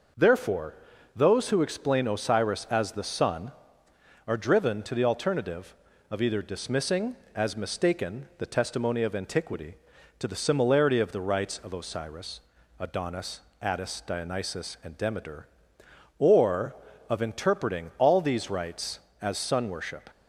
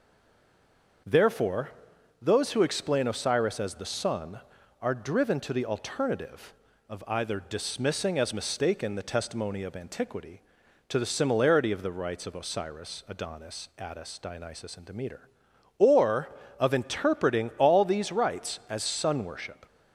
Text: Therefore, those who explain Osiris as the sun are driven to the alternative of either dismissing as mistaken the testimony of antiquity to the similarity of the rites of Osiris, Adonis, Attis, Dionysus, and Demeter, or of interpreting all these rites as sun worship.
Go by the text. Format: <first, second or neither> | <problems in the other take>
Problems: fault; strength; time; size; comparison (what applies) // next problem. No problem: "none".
first | stays silent before the first word; until 1.0 s; 1.0 s long // starts louder than the rest; until 2.5 s; 6 dB